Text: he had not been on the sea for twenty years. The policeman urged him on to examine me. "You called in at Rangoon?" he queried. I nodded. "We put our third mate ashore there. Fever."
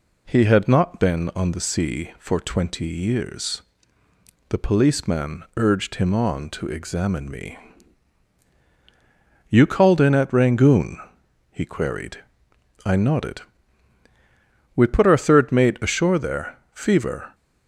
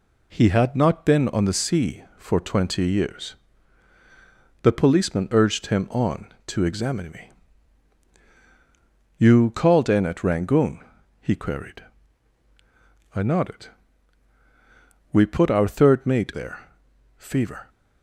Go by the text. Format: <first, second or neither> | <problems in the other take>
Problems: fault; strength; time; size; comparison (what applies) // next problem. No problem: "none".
first | skips "ashore"; at 16.3 s